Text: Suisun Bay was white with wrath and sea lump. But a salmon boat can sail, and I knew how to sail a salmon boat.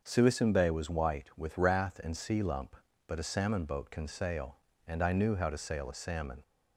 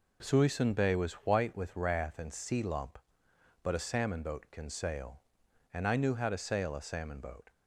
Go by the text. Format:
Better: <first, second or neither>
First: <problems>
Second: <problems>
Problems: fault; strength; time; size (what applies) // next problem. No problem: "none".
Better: second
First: starts louder than the rest; until 1.0 s; 6.5 dB // stops before "boat"; at 6.4 s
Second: none